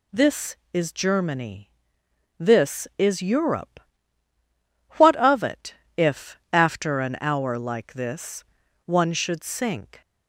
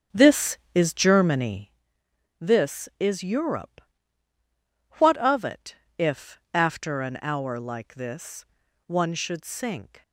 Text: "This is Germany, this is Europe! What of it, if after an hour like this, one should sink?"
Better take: first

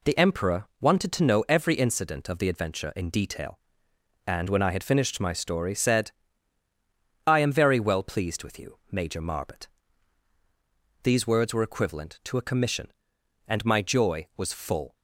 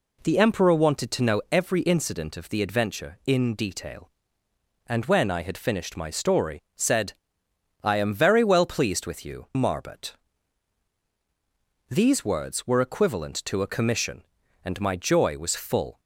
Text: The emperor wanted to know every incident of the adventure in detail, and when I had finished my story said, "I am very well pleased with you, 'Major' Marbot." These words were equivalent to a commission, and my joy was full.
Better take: first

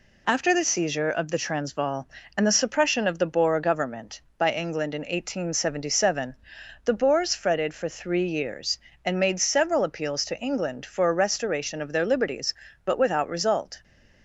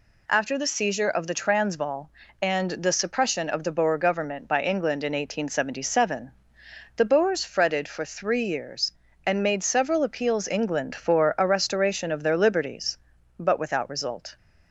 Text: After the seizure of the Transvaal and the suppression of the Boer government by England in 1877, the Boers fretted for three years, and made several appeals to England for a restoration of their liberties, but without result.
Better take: first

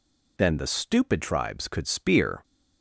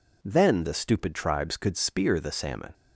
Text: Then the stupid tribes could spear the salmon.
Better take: second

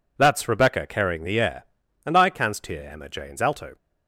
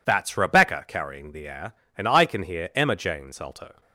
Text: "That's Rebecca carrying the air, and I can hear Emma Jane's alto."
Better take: second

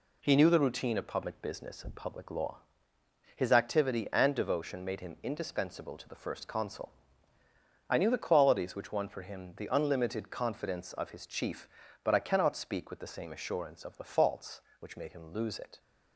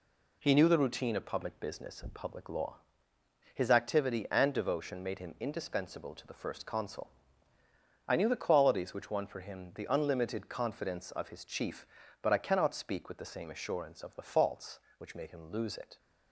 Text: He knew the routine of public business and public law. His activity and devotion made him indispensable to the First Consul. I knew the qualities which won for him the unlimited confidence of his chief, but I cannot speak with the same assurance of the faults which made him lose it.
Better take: neither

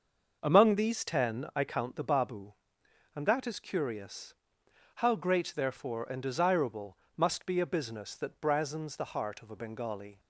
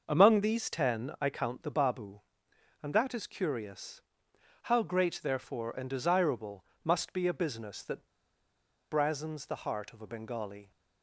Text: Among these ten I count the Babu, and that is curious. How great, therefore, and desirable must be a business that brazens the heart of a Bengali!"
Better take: first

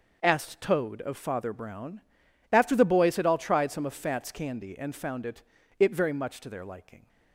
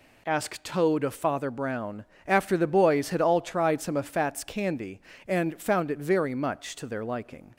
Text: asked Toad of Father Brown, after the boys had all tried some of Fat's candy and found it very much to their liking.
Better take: second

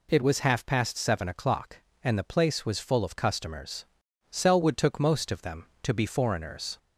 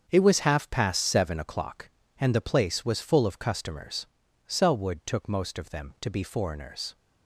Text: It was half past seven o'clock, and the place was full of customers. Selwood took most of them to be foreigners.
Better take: first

